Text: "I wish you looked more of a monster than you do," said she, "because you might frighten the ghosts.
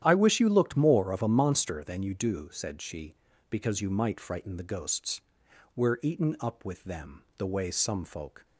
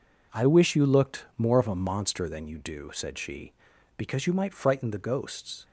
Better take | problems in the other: second | starts louder than the rest; strong; until 1.0 s; 10.5 dB // goes on to say "We're eaten up with them the way some folk"; strong; from 5.7 s on; 2.6 s long

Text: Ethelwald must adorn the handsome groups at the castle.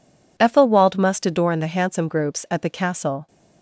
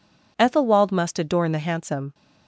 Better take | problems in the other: first | stops before "groups at the castle"; at 2.1 s

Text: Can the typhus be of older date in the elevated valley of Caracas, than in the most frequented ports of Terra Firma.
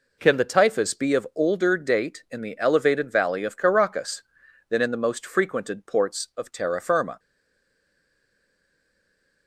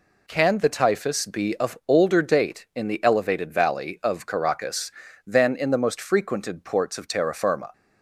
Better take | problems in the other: second | stays silent after the last word; from 7.1 s on; 2.3 s long

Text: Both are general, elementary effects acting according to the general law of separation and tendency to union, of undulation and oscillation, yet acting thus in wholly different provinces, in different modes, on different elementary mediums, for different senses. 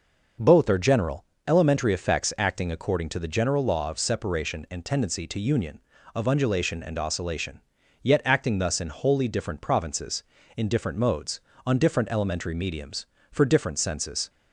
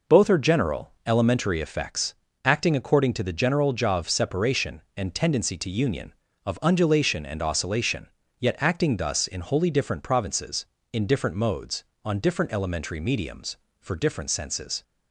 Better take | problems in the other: first | pauses between "effects" and "acting"; slight; at 2.1 s; 0.30 s long // says "jaw" for "law"; at 3.7 s

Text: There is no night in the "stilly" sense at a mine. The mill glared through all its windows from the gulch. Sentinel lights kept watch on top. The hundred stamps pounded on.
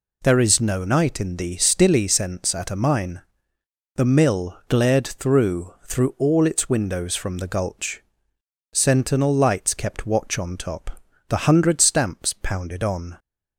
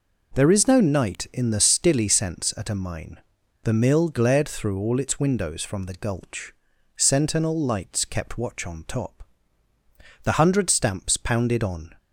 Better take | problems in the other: second | says "through" twice; at 5.8 s

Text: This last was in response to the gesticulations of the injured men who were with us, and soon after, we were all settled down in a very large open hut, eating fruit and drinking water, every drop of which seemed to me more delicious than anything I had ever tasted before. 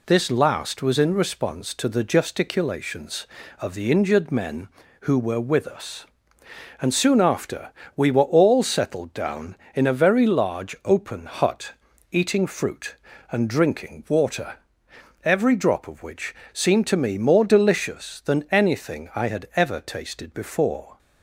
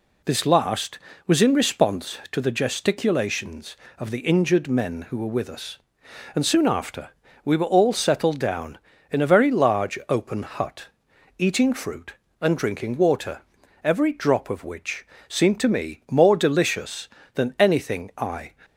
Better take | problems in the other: first | pauses between "which" and "seemed"; slight; at 15.0 s; 0.22 s long; slight in the first // stops before "had ever tasted before"; at 18.6 s

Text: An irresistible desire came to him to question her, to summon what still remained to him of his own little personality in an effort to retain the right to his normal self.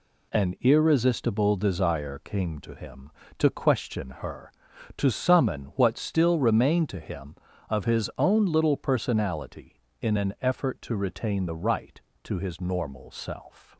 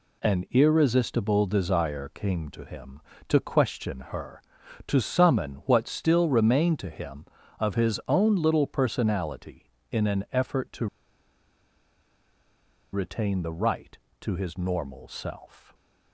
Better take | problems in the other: first | pauses between "to" and "retain"; strong; at 10.8 s; 2.0 s long

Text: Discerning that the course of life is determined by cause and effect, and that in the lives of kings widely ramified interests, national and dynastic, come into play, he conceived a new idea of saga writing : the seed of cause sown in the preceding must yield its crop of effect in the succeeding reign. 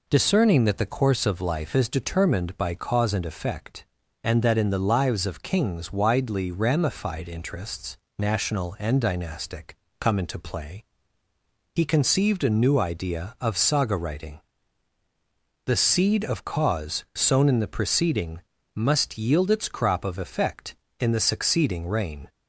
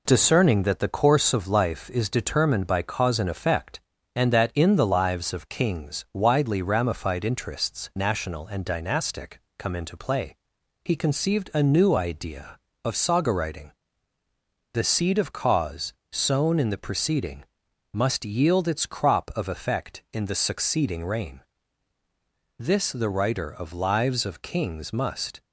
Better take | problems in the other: first | pauses between "cause" and "sown"; slight; at 15.9 s; 0.20 s long // pauses between "preceding" and "must"; noticeable; at 17.4 s; 0.48 s long; slight in the first // goes on to say "This the writer of lives of kings must"; strong; from 22.5 s on; 2.8 s long

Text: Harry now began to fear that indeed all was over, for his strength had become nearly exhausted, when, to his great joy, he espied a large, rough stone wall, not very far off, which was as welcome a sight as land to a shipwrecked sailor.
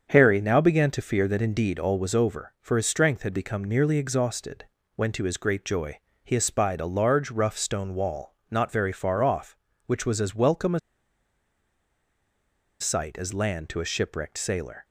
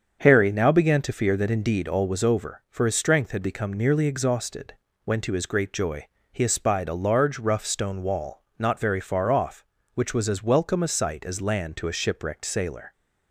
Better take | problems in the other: second | starts louder than the rest; until 1.1 s; 7 dB; also in the second // pauses between "a" and "sight"; strong; at 10.7 s; 2.0 s long

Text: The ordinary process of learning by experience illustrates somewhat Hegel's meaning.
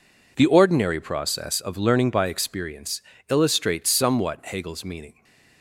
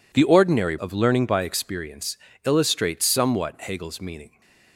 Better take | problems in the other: first | skips "process"; at 0.7 s // pauses between "experience" and "illustrates"; slight; at 2.1 s; 0.28 s long; slight in the first

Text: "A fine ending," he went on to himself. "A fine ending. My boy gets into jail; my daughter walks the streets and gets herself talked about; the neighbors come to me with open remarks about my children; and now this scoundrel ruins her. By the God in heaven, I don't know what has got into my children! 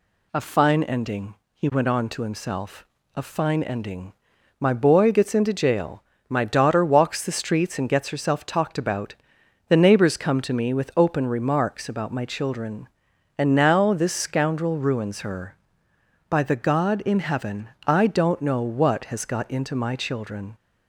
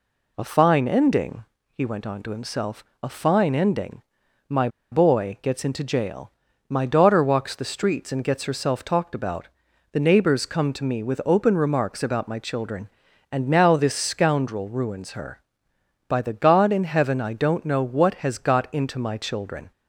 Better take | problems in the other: first | pauses between "My" and "boy"; slight; at 4.6 s; 0.23 s long

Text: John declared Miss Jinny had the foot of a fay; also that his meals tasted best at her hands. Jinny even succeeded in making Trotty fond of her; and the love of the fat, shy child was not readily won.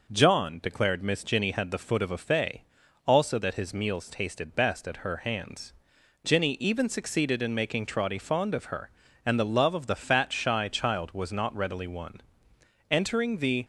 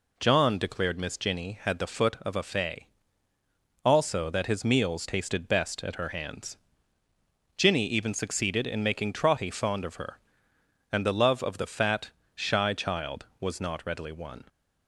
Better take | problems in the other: second | goes on to say "Entering the"; noticeable; from 12.9 s on; 0.74 s long

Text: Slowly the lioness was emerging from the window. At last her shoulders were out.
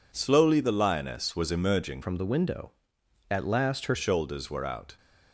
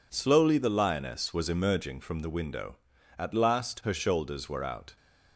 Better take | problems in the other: second | changes voice from "from" to "her"; from 2.0 to 3.9 s; 1.9 s long

